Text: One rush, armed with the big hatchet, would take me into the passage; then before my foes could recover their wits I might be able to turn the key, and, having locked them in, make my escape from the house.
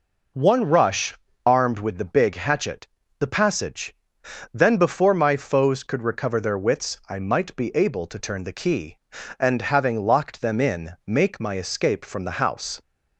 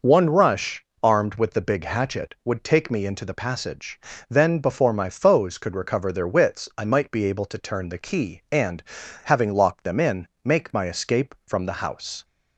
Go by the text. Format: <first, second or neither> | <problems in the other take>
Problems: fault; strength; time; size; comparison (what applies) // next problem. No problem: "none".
second | skips "would take me into"; at 3.0 s